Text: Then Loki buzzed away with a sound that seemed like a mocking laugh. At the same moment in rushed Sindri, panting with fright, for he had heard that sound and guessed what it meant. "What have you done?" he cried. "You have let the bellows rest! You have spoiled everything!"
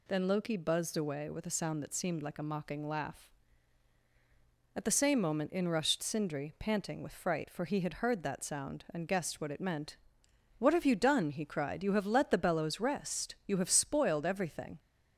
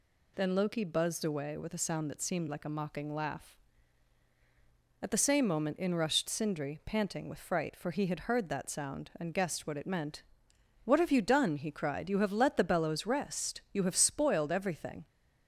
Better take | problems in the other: neither | none

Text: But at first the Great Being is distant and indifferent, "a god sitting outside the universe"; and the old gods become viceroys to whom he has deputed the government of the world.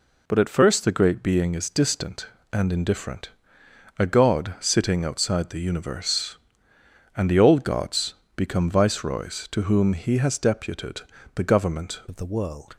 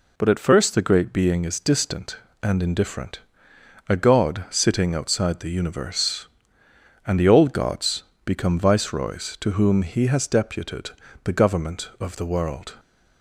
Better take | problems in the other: second | pauses between "gods" and "become"; slight; at 8.1 s; 0.24 s long; slight in the second // pauses between "deputed" and "the"; slight; at 11.0 s; 0.34 s long; slight in the second // changes voice at "of"; from 12.0 s on; 0.7 s long

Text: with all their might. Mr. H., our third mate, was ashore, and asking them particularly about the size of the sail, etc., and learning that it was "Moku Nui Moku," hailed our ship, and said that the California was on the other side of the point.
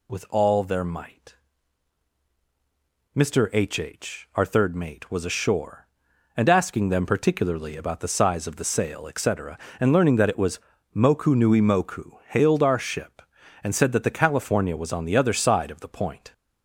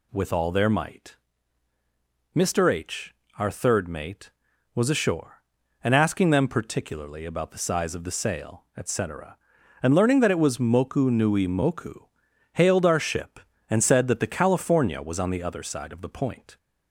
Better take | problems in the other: second | says "H" twice; at 3.7 s // pauses between "was" and "Moku"; slight; at 10.5 s; 0.36 s long

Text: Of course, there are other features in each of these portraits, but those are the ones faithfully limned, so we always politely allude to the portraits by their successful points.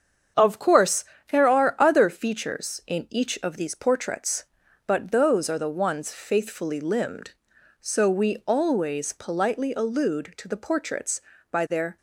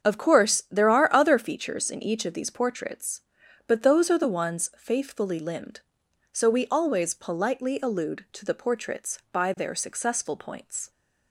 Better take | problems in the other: second | starts louder than the rest; strong; until 1.6 s; 7.5 dB; strong in the second // stops before "successful points"; at 11.9 s

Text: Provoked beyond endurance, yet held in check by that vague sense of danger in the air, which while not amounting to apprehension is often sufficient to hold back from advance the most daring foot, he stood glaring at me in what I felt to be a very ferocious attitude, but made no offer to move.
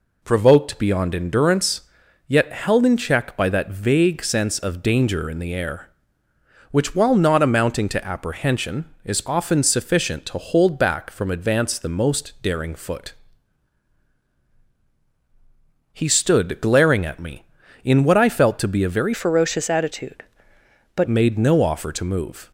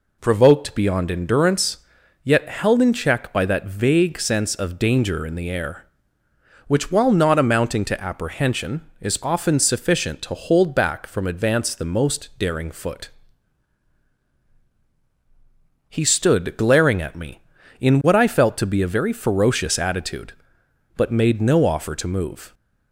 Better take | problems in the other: second | changes voice from "ferocious" to "but"; from 19.1 to 21.0 s; 1.9 s long

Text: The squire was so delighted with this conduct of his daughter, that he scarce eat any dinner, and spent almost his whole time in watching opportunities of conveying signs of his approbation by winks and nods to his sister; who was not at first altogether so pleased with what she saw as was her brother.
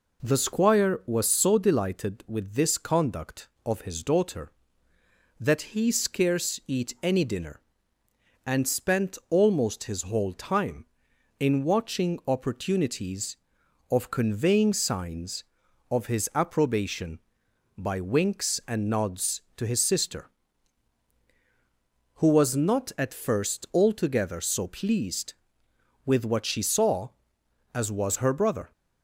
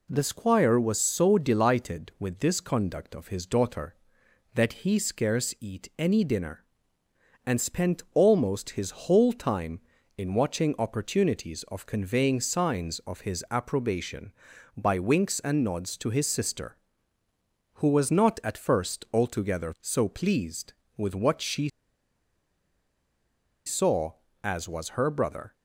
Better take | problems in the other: first | pauses between "she" and "saw"; strong; at 21.6 s; 1.9 s long

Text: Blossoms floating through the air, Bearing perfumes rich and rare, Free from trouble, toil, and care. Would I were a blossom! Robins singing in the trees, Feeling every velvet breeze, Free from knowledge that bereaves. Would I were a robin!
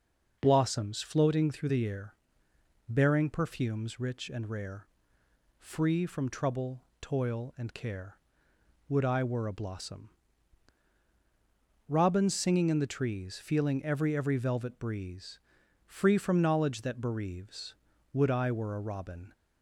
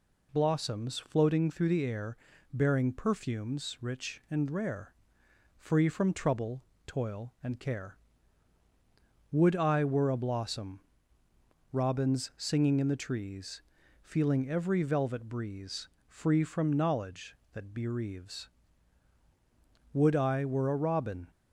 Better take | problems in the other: second | says "every" twice; at 14.1 s

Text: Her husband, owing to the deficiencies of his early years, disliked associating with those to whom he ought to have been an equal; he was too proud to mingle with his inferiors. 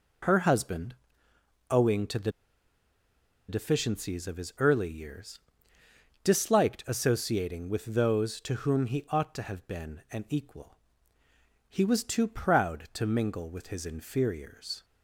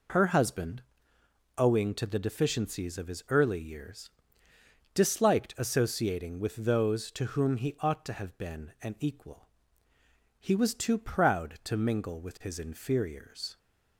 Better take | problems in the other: second | pauses between "the" and "deficiencies"; at 2.3 s; 1.1 s long

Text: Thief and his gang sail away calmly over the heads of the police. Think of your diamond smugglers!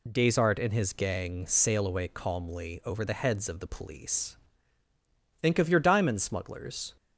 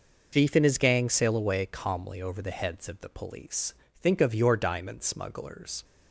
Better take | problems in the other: second | says "Desart" for "Thief"; at 0.1 s

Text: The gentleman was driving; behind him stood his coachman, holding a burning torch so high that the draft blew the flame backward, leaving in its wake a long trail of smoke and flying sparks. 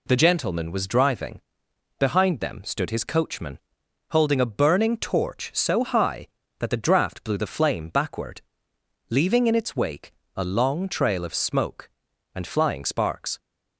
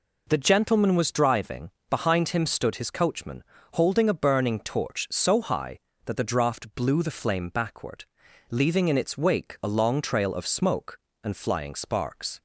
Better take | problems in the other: second | says "them" for "him"; at 2.3 s // pauses between "wake" and "a"; slight; at 10.1 s; 0.24 s long

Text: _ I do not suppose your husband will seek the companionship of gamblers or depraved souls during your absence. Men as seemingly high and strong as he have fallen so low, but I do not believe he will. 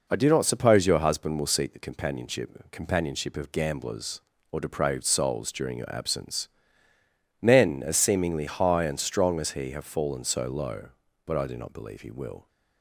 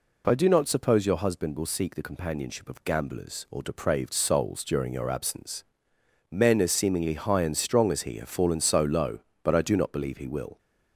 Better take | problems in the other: second | says "companionship" twice; at 2.7 s

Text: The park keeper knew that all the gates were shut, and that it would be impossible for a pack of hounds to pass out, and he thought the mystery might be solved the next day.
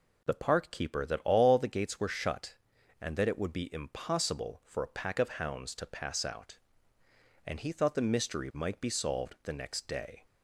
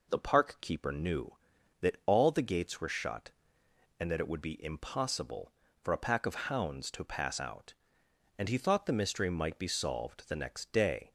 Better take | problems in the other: second | skips "knew"; at 1.0 s

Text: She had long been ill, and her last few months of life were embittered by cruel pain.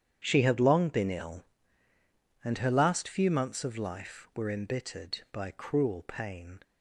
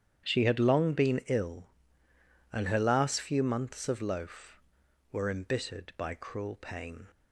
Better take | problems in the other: first | starts louder than the rest; strong; until 1.3 s; 9.5 dB; strong in the first // says "loaf" for "life"; at 4.0 s

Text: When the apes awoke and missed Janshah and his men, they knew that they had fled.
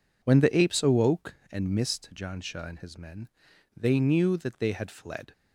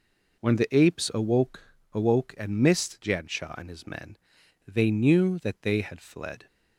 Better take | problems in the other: first | says "awoke" twice; at 1.9 s

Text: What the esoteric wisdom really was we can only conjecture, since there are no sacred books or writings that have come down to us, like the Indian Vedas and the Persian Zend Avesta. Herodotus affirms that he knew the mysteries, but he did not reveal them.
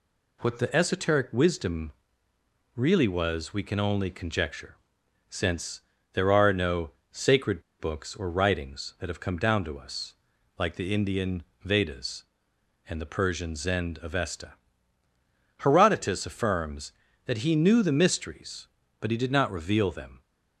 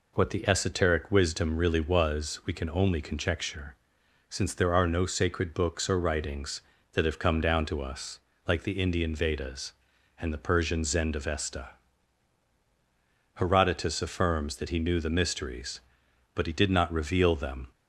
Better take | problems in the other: second | pauses between "wisdom" and "really"; noticeable; at 1.9 s; 0.82 s long // pauses between "since" and "there"; slight; at 5.8 s; 0.32 s long // pauses between "no" and "sacred"; slight; at 6.9 s; 0.20 s long // pauses between "sacred" and "books"; slight; at 7.6 s; 0.18 s long // pauses between "Indian" and "Vedas"; slight; at 11.4 s; 0.20 s long

